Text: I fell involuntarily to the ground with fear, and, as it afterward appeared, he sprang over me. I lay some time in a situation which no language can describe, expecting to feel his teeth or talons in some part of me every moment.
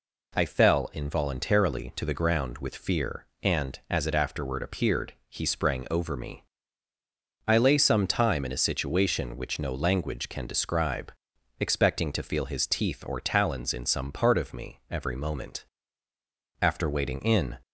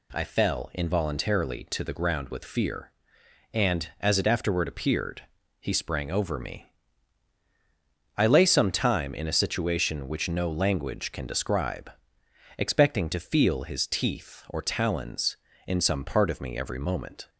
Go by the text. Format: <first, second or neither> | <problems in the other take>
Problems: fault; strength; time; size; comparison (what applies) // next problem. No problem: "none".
second | goes on to say "After waiting in"; noticeable; from 16.6 s on; 0.96 s long